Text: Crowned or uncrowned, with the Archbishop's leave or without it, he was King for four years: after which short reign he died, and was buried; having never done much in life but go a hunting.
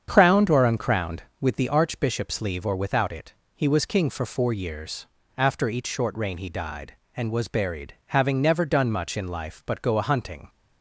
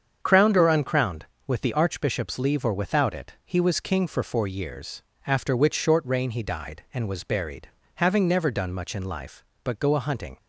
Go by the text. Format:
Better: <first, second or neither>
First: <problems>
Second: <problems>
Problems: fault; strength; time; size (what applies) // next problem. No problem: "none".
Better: second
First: starts louder than the rest; strong; until 1.1 s; 7.5 dB // says "each" for "which"; at 5.6 s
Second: starts louder than the rest; strong; until 1.2 s; 7 dB